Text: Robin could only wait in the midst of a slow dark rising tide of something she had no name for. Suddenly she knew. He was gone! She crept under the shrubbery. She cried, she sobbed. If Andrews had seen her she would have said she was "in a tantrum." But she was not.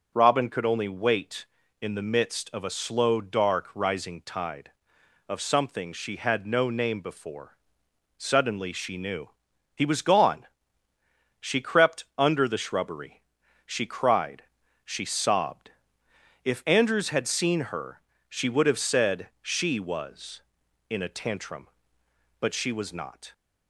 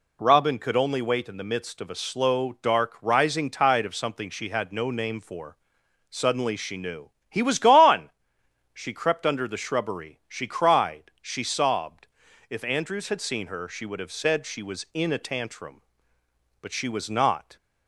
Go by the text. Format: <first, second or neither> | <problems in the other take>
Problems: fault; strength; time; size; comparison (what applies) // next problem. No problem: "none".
second | says "before" for "for"; at 7.0 s // pauses between "her" and "she"; slight; at 17.9 s; 0.30 s long // pauses between "said" and "she"; slight; at 19.2 s; 0.16 s long